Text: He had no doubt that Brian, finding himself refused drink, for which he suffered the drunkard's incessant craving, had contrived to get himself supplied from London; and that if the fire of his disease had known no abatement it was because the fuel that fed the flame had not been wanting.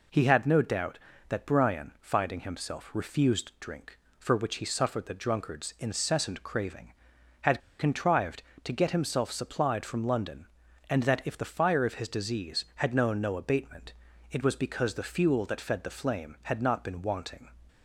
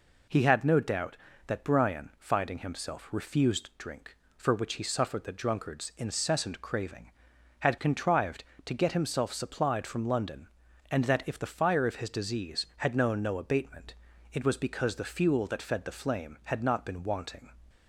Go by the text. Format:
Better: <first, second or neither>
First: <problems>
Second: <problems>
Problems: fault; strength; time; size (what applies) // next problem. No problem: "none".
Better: second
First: pauses between "had" and "contrived"; slight; at 7.5 s; 0.19 s long // pauses between "abatement" and "it"; slight; at 13.9 s; 0.36 s long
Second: pauses between "abatement" and "it"; slight; at 13.9 s; 0.36 s long